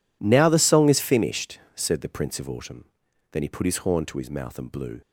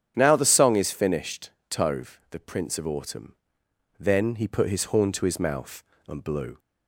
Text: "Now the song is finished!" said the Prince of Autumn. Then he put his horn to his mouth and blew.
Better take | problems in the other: first | starts louder than the rest; strong; until 1.1 s; 9 dB // says "tove" for "said"; at 1.6 s

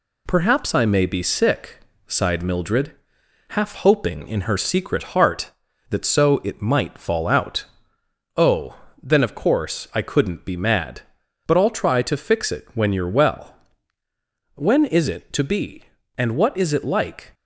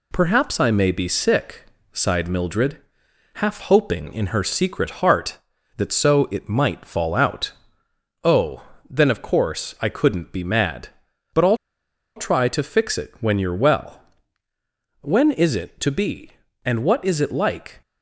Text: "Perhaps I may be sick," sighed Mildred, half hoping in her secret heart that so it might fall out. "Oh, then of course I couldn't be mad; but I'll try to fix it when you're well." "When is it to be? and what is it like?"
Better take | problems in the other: first | pauses between "I'll" and "try"; noticeable; at 11.5 s; 0.59 s long

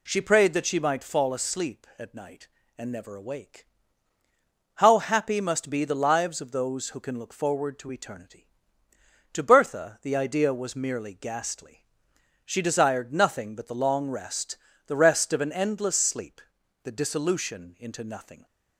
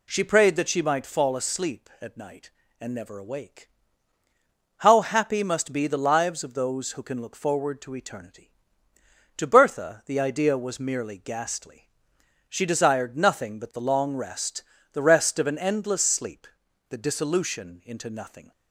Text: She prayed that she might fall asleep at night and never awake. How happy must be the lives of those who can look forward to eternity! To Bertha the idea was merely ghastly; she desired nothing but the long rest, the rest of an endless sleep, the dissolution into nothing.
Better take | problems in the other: neither | none

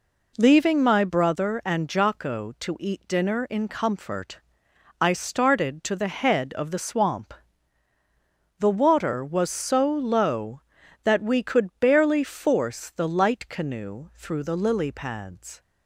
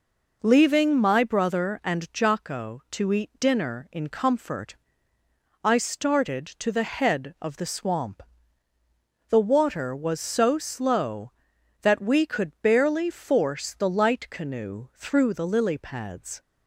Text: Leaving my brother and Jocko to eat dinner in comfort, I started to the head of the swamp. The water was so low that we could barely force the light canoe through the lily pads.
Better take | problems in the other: first | says "slow" for "low"; at 10.5 s

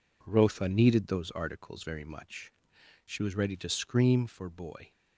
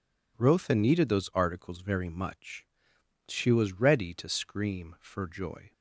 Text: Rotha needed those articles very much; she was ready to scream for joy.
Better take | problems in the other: second | says "boy" for "joy"; at 4.5 s

